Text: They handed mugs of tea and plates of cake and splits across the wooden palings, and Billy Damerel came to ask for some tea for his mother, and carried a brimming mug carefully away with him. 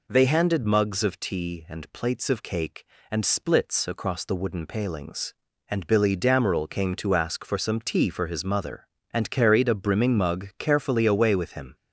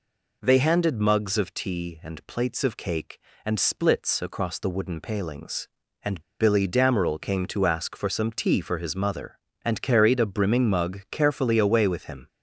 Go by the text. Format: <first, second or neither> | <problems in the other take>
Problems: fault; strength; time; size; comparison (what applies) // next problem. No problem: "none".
first | pauses between "and" and "Billy"; slight; at 6.1 s; 0.19 s long